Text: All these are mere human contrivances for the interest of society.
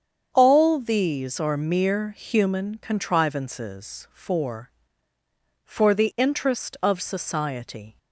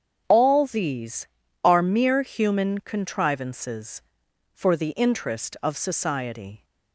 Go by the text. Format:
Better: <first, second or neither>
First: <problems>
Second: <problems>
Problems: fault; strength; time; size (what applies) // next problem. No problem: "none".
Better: second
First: starts louder than the rest; strong; until 1.3 s; 7.5 dB // says "for" twice; at 5.6 s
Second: starts louder than the rest; strong; until 1.2 s; 7.5 dB